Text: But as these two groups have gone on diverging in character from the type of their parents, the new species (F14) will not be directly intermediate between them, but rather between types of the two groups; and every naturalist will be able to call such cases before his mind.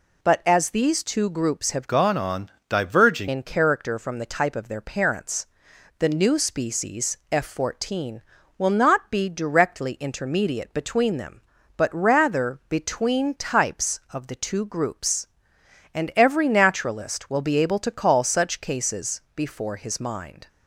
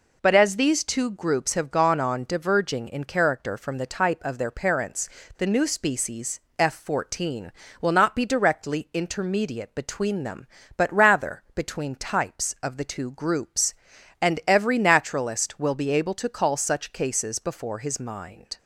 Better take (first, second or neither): second